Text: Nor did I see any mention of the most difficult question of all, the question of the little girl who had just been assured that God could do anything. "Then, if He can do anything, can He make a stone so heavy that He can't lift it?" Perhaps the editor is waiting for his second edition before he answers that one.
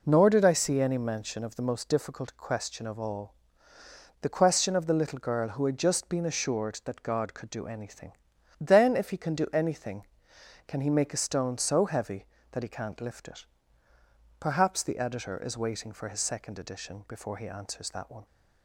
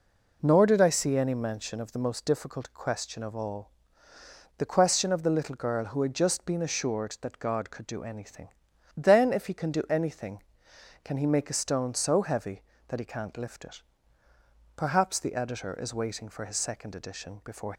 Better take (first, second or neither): first